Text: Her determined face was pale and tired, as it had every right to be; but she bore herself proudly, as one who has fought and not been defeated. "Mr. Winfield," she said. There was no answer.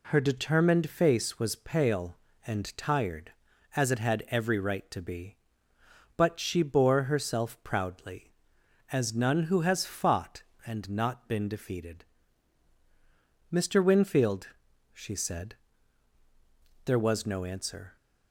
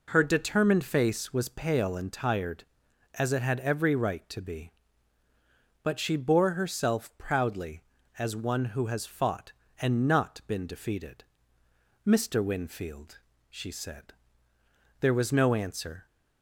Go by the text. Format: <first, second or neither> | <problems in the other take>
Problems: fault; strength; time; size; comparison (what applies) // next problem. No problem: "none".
second | says "none" for "one"; at 9.1 s